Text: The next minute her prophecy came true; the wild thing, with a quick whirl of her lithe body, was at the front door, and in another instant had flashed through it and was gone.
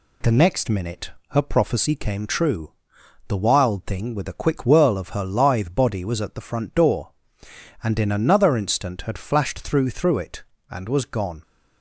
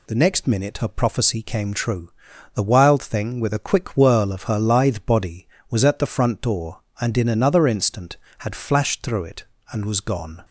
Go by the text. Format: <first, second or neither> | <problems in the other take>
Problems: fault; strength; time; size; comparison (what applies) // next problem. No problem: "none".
second | pauses between "minute" and "her"; slight; at 1.0 s; 0.20 s long // says "through" twice; at 9.8 s